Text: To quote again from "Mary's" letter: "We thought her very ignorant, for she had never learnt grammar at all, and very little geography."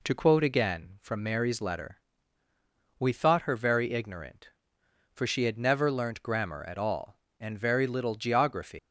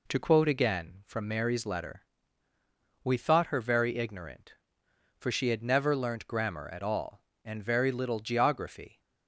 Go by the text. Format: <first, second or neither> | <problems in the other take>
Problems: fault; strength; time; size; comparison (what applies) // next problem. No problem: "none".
second | leaves "geography" unfinished; at 8.7 s; 170 ms